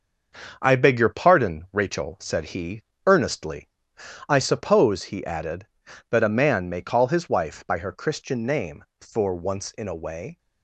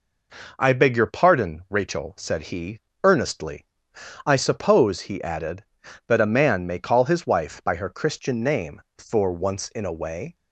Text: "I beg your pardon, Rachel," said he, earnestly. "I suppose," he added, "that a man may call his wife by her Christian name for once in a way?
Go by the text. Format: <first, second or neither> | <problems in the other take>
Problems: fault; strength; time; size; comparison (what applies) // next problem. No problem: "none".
second | gets quieter; throughout; 7 dB